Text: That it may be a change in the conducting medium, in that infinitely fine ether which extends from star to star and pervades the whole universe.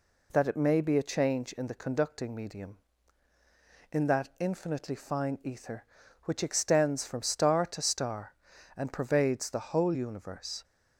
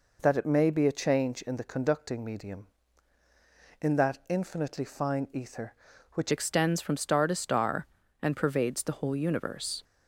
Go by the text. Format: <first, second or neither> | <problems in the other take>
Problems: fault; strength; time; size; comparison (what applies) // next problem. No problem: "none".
first | changes voice at "extends"; from 6.3 s on; 3.5 s long